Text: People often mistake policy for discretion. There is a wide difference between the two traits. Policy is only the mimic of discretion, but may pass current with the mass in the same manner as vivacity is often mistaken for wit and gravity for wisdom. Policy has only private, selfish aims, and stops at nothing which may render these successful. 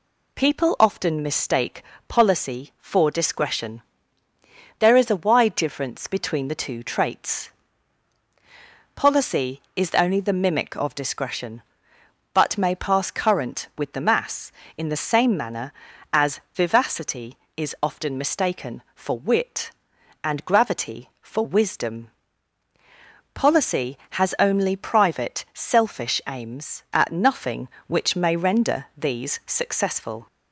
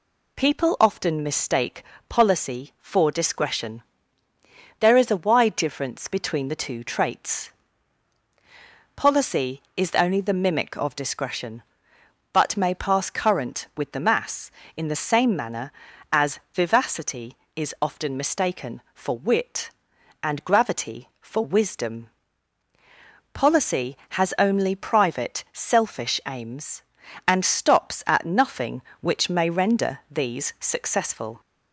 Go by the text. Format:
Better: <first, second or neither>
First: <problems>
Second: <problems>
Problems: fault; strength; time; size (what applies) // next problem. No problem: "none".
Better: second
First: pauses between "mistake" and "policy"; slight; at 1.8 s; 0.24 s long // skips "and stops"; at 26.8 s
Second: pauses between "mistake" and "policy"; slight; at 1.8 s; 0.24 s long